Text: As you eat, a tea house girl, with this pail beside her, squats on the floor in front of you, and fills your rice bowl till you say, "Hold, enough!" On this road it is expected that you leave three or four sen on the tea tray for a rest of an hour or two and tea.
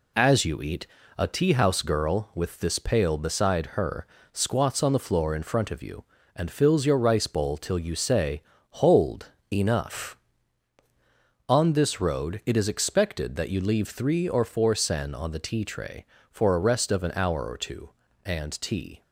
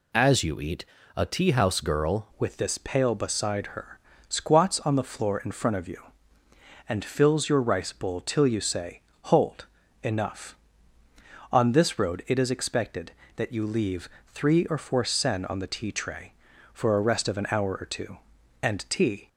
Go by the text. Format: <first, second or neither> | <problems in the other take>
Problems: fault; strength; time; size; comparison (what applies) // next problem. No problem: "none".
first | changes voice at "with"; from 2.3 s on; 16.9 s long // pauses between "leave" and "three"; slight; at 14.0 s; 0.20 s long